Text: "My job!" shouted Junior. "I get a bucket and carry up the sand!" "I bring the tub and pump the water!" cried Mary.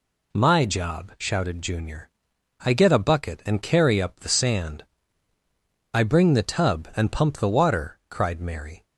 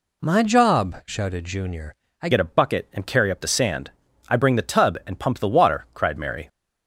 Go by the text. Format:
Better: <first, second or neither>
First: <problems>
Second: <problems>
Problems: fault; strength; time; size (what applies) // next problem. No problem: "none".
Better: first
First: none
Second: changes voice at "get"; from 2.3 s on; 4.1 s long